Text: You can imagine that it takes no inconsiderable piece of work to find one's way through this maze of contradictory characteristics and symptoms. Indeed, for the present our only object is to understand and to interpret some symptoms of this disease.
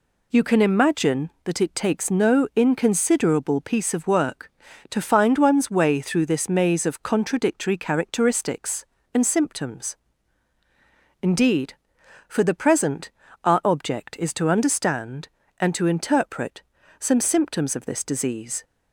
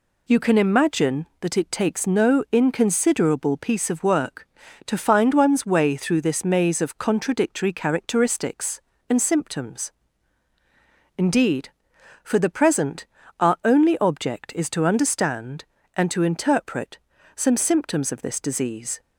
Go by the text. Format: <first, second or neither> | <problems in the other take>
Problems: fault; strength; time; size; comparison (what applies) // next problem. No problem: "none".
second | pauses between "present" and "our"; slight; at 13.1 s; 0.32 s long; slight in the second // skips "only"; at 13.6 s // pauses between "interpret" and "some"; at 16.6 s; 0.38 s long; also in the second